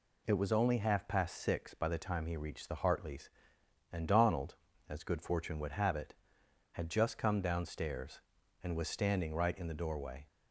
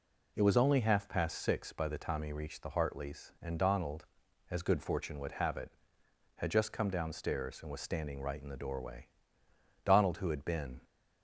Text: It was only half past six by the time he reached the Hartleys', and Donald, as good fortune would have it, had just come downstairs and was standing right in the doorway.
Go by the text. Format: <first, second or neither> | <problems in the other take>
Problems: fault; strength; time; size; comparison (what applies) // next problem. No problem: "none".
first | goes on to say "Donald who had been"; noticeable; from 9.8 s on; 0.96 s long